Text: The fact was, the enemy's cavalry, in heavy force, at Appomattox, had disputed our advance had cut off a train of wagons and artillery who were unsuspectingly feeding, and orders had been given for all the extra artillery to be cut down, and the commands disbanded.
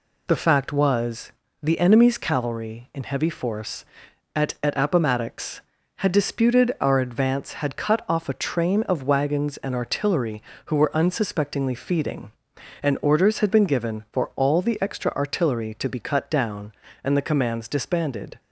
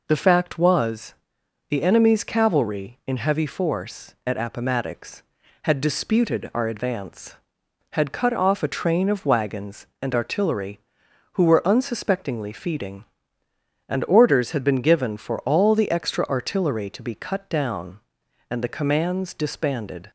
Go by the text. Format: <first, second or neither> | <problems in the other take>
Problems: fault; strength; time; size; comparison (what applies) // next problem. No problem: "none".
second | says "at" twice; at 4.6 s